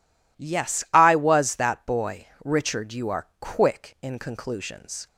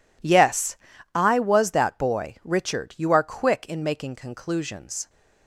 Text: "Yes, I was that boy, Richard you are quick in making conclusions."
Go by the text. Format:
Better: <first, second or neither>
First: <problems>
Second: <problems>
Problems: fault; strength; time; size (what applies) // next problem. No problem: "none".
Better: second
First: skips "making"; at 4.1 s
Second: none